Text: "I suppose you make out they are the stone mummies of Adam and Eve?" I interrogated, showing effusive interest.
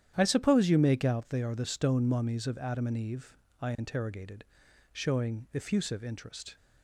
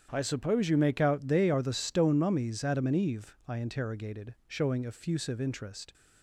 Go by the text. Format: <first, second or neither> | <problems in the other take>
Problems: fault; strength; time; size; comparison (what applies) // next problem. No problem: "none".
first | starts louder than the rest; strong; until 1.1 s; 9 dB; strong in the first // skips "of"; at 2.6 s